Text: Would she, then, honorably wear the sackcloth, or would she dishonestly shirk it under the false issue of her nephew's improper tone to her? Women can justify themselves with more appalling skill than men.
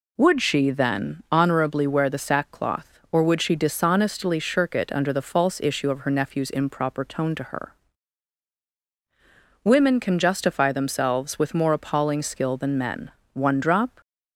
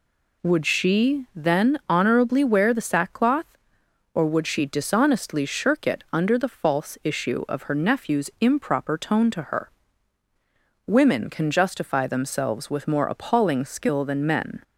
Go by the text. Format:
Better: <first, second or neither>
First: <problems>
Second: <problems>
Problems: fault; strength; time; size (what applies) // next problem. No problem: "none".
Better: second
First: goes on to say "One drop"; noticeable; from 13.3 s on; 0.66 s long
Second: none